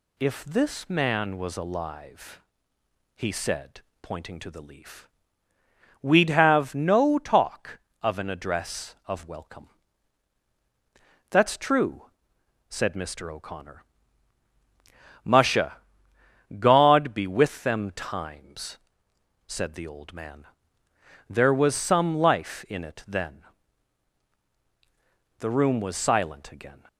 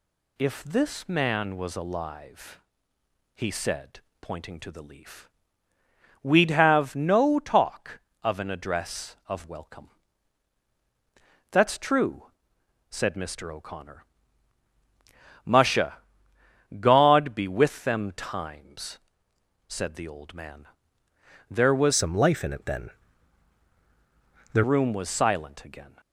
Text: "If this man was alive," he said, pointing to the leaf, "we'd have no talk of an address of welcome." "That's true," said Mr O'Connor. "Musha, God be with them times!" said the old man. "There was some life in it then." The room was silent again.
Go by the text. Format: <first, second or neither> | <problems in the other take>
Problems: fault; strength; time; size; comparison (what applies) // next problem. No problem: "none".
first | changes voice from "some" to "The"; from 21.9 to 24.6 s; 2.7 s long